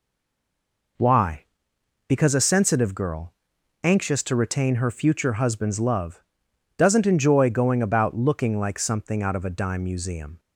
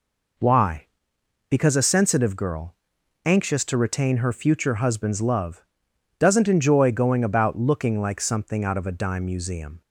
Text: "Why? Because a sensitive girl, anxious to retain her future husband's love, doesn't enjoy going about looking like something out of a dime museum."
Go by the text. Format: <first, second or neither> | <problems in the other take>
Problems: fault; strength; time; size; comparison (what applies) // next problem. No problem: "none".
second | stays silent before the first word; until 0.9 s; 0.9 s long